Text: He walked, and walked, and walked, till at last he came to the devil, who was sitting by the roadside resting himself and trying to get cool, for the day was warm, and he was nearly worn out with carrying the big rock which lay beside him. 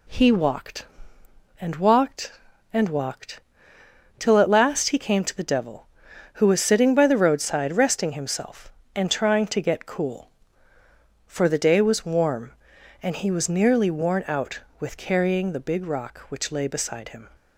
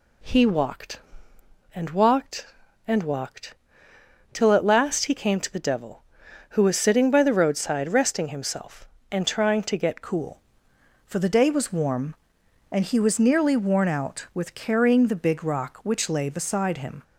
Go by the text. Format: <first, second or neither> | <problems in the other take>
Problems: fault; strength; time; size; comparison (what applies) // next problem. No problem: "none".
first | changes voice at "cool"; from 10.0 s on; 7.0 s long